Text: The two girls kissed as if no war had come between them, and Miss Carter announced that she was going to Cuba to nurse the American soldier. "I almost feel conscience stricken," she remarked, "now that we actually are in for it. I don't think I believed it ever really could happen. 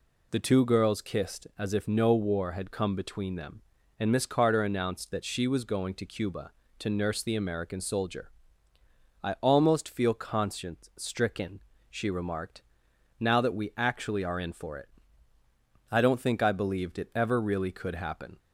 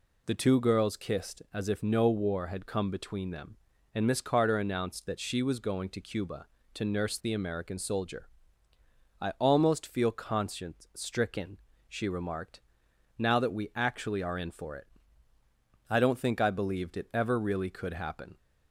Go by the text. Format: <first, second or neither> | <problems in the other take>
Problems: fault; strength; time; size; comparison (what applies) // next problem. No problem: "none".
neither | none